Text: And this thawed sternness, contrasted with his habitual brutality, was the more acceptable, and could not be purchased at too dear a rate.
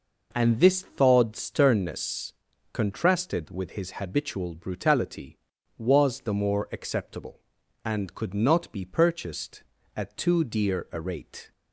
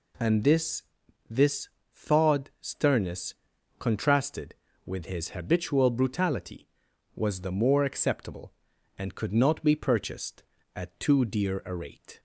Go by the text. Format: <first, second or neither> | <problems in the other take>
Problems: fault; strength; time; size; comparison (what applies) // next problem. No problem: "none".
first | says "this" twice; at 1.2 s